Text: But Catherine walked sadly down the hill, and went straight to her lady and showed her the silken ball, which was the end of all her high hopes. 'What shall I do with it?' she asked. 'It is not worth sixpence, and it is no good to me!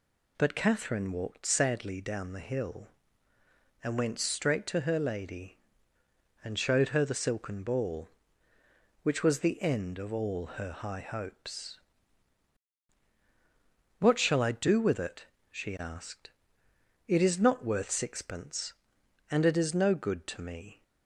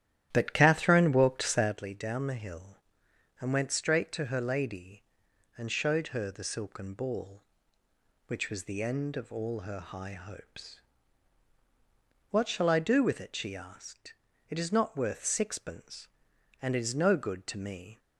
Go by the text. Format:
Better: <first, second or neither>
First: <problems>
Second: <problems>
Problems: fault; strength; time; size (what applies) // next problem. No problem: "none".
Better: first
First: none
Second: starts louder than the rest; strong; until 1.8 s; 12 dB